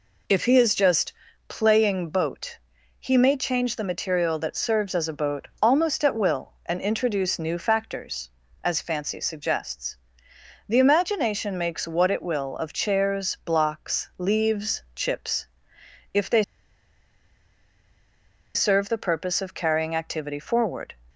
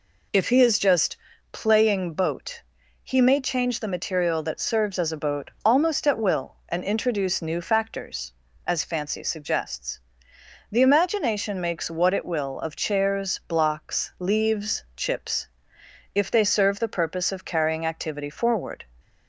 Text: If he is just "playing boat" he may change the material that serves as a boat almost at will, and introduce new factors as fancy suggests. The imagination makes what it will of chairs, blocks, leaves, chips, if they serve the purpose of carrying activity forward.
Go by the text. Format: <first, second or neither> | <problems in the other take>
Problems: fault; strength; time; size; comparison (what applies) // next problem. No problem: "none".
second | pauses between "just" and "playing"; slight; at 1.1 s; 0.34 s long; slight in the second // pauses between "boat" and "he"; at 2.5 s; 0.40 s long; also in the second // pauses between "they" and "serve"; strong; at 16.4 s; 2.1 s long